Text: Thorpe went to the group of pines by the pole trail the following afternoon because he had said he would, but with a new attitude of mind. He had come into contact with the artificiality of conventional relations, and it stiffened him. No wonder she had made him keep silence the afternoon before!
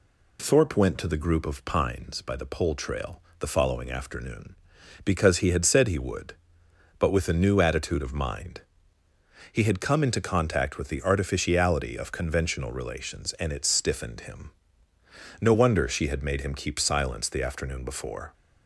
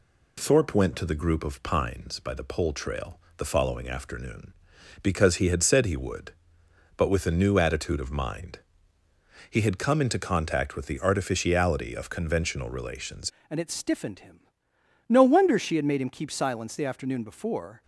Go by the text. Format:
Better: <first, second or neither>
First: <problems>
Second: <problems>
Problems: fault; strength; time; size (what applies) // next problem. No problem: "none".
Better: first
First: pauses between "trail" and "the"; slight; at 3.2 s; 0.20 s long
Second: pauses between "trail" and "the"; slight; at 3.1 s; 0.20 s long // changes voice at "and"; from 13.4 s on; 4.4 s long